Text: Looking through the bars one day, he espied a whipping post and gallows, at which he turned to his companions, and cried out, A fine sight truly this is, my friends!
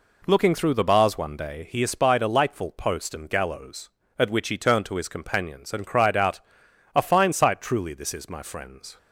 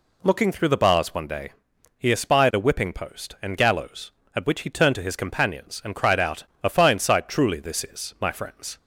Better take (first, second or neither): second